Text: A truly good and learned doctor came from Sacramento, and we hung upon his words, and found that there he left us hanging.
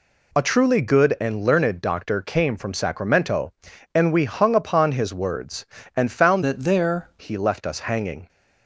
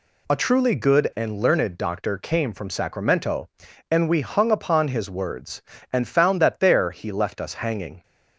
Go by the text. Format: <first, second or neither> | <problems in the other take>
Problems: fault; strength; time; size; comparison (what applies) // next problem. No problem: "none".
second | changes voice from "that" to "there"; from 6.4 to 7.0 s; 0.6 s long